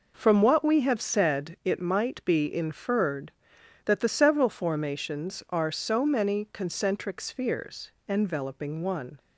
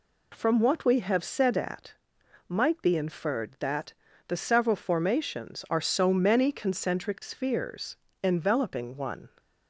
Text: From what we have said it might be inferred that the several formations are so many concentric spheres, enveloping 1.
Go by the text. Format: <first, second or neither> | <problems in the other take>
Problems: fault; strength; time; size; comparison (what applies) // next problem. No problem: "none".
first | says "at" for "it"; at 1.5 s // pauses between "that" and "the"; slight; at 3.9 s; 0.36 s long